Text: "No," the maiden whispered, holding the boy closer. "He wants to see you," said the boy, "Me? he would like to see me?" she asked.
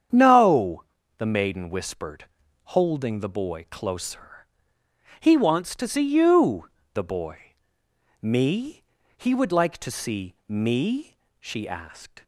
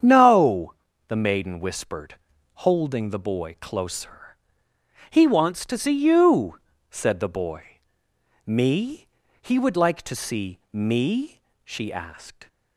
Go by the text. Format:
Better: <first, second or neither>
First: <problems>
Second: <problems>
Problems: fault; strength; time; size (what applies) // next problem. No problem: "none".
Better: second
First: starts louder than the rest; strong; until 1.4 s; 8 dB // skips "said"; at 6.8 s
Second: starts louder than the rest; strong; until 1.3 s; 8 dB